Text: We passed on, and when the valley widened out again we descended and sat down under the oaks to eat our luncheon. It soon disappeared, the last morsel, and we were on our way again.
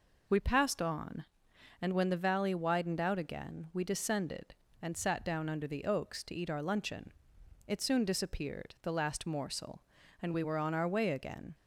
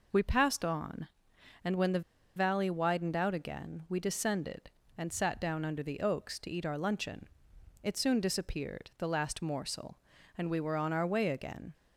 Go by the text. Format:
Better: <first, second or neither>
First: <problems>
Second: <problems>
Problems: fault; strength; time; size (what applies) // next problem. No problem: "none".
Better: first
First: none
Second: pauses between "the" and "valley"; slight; at 2.0 s; 0.35 s long